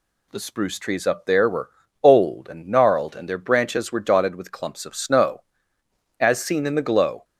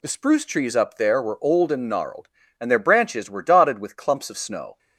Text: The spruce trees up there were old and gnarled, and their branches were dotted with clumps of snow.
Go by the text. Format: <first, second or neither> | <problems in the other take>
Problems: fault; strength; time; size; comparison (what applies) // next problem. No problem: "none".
second | pauses between "were" and "old"; slight; at 1.7 s; 0.32 s long // goes on to say "As seen in the glow"; noticeable; from 6.2 s on; 1.0 s long